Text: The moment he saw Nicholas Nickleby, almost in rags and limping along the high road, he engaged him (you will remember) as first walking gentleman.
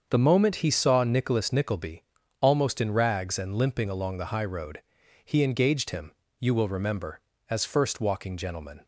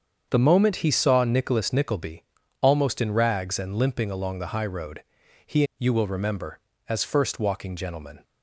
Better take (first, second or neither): first